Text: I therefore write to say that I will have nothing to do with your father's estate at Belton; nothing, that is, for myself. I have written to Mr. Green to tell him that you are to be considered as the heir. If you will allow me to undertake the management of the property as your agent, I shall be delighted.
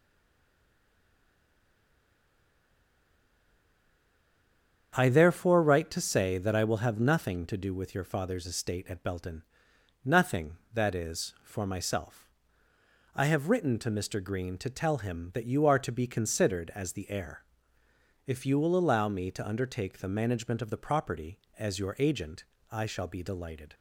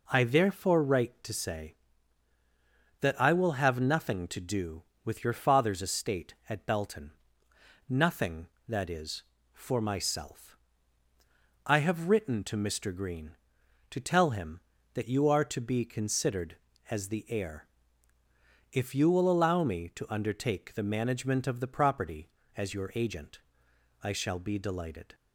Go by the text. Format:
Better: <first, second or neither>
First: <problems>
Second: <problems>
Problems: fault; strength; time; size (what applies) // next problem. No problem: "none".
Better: second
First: stays silent before the first word; strong; until 4.9 s; 4.9 s long // starts louder than the rest; strong; until 5.9 s; 8 dB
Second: none